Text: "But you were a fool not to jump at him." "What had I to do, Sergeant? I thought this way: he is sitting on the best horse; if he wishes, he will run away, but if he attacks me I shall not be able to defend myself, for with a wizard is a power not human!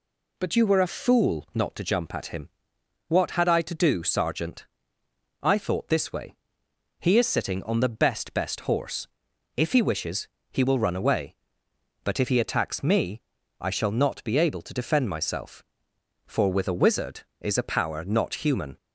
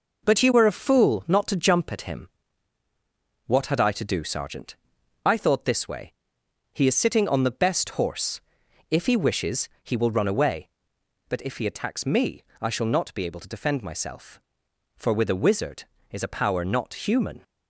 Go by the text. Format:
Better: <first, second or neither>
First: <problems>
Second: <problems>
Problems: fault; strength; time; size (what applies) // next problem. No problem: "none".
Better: second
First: says "best" twice; at 8.3 s // pauses between "me" and "I"; at 13.2 s; 0.40 s long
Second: pauses between "me" and "I"; slight; at 12.4 s; 0.16 s long